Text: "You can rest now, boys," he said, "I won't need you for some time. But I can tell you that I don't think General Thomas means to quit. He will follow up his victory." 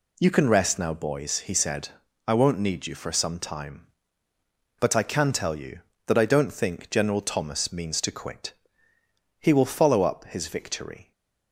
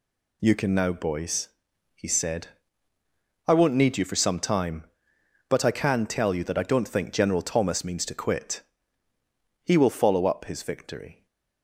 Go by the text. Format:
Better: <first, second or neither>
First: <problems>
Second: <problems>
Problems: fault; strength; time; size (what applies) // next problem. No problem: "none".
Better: first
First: none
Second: skips "rest"; at 0.7 s // stays silent after the last word; slight; from 11.1 s on; 0.5 s long